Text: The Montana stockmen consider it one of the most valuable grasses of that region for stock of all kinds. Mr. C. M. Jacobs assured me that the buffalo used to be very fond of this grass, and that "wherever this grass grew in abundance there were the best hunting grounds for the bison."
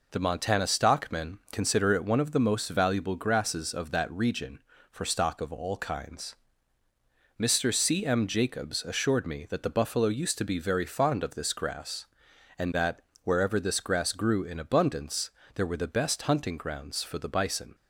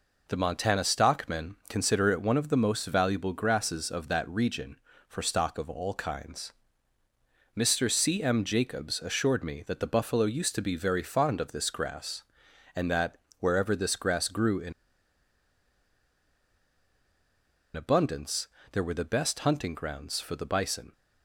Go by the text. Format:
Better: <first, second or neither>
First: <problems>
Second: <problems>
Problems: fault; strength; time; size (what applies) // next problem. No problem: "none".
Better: first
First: pauses between "that" and "wherever"; slight; at 13.0 s; 0.22 s long // pauses between "abundance" and "there"; slight; at 15.2 s; 0.26 s long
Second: pauses between "that" and "wherever"; slight; at 13.1 s; 0.22 s long // pauses between "in" and "abundance"; strong; at 14.7 s; 3.0 s long // pauses between "abundance" and "there"; slight; at 18.4 s; 0.26 s long